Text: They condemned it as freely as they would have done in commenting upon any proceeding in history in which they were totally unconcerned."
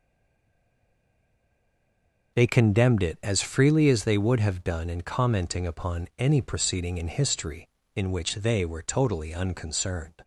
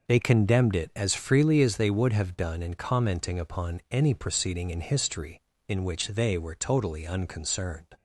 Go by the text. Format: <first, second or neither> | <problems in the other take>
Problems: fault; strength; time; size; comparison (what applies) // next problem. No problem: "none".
second | stays silent before the first word; until 2.3 s; 2.3 s long